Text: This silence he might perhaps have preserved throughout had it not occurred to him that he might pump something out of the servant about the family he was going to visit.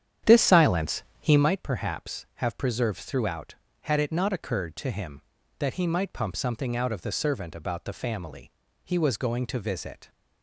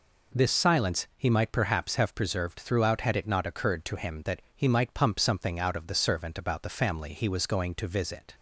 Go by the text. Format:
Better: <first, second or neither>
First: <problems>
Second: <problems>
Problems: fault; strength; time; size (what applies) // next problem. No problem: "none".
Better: second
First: starts louder than the rest; strong; until 1.5 s; 9.5 dB // pauses between "silence" and "he"; slight; at 1.0 s; 0.18 s long // pauses between "family" and "he"; slight; at 8.4 s; 0.36 s long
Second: none